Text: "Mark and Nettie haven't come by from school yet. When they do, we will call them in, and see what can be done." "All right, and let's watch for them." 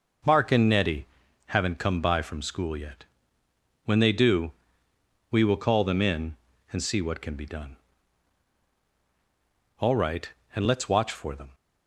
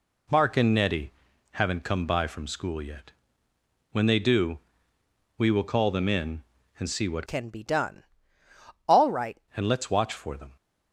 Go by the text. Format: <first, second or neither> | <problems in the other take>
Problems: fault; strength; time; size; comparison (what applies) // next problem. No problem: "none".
first | pauses between "Nettie" and "haven't"; at 1.1 s; 0.42 s long; also in the first // changes voice from "can" to "right"; from 7.2 to 9.3 s; 2.1 s long